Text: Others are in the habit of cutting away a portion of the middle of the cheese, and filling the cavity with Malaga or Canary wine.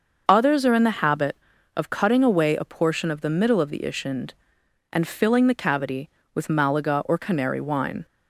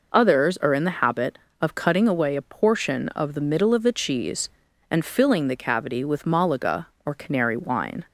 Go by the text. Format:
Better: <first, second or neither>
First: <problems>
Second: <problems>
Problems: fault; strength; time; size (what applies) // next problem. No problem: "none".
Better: second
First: starts louder than the rest; noticeable; until 1.2 s; 6 dB // says "ishind" for "cheese"; at 3.7 s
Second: none